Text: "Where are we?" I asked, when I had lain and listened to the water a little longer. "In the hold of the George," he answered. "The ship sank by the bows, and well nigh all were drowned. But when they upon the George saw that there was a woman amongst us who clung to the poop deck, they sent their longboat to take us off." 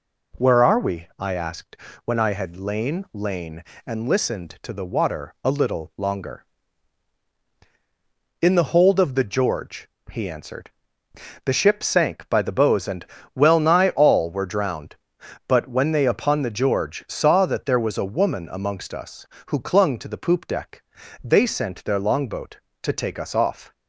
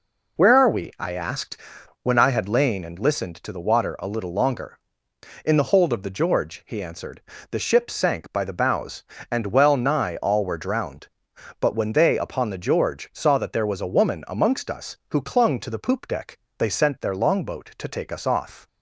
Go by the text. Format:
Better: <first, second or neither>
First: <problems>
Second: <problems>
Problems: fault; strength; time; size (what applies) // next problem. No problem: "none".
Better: second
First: says "lain" twice; at 3.1 s // pauses between "and" and "well"; slight; at 13.0 s; 0.30 s long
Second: none